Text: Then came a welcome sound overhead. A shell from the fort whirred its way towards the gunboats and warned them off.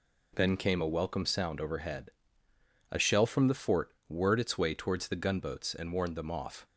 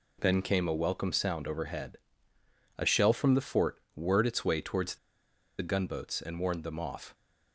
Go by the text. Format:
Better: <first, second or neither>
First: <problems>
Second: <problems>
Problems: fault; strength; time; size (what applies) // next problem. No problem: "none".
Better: first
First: pauses between "fort" and "whirred"; slight; at 3.9 s; 0.16 s long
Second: pauses between "fort" and "whirred"; slight; at 3.7 s; 0.16 s long // pauses between "the" and "gunboats"; noticeable; at 4.9 s; 0.63 s long